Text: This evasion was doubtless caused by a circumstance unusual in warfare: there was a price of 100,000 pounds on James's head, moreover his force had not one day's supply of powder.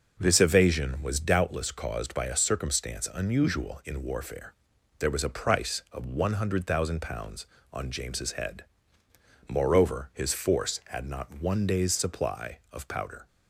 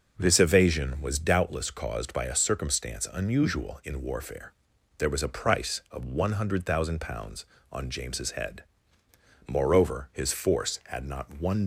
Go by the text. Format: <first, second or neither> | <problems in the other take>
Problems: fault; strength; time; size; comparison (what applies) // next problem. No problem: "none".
first | stops before "day's supply of powder"; at 11.6 s